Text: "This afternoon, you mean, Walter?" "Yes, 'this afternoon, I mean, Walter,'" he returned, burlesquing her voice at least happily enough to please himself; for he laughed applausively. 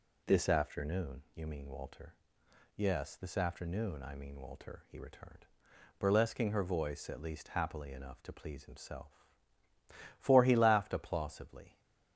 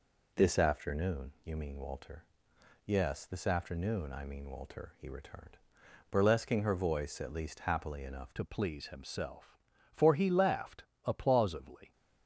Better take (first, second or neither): first